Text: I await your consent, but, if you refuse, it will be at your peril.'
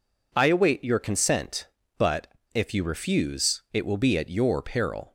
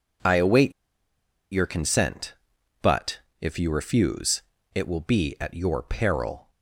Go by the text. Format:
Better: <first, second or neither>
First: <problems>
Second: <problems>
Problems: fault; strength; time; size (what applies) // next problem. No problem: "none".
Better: first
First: none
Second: pauses between "await" and "your"; noticeable; at 0.7 s; 0.80 s long